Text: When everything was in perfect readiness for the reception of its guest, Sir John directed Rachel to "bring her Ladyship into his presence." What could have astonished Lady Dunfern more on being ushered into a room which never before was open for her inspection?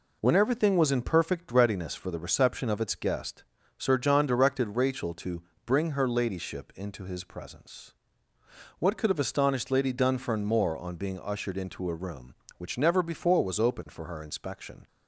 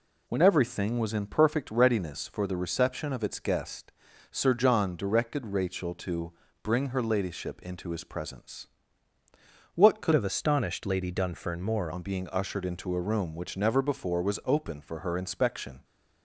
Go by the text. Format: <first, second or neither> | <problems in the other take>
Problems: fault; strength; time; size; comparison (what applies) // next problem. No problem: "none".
first | pauses between "to" and "bring"; slight; at 6.3 s; 0.28 s long; slight in the first // changes voice from "have" to "more"; from 10.1 to 11.9 s; 1.8 s long